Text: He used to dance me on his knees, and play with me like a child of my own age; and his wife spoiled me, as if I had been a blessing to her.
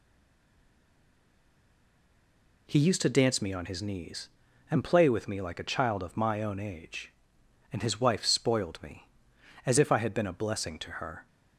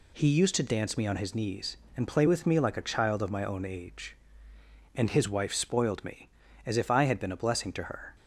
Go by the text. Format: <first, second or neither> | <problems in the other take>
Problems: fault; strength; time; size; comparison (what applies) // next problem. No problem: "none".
second | stays silent before the first word; strong; until 2.6 s; 2.6 s long